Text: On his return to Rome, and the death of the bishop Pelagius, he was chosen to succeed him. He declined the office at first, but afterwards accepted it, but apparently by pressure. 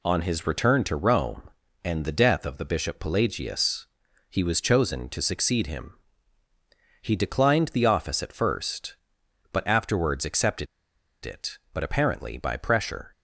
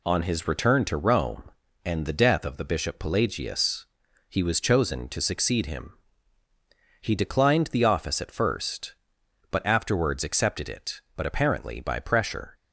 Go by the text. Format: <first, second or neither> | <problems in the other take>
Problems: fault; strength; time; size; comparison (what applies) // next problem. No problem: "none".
second | pauses between "accepted" and "it"; noticeable; at 10.6 s; 0.58 s long